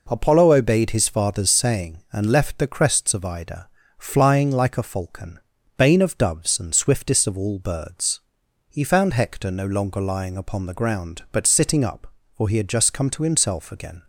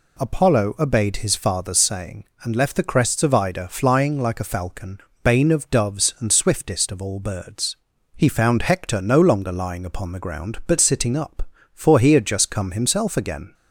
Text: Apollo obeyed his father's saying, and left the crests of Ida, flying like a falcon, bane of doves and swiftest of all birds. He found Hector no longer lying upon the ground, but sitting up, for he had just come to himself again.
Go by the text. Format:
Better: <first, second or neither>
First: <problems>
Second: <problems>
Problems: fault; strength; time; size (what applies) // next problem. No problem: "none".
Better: first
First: none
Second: skips "to"; at 12.7 s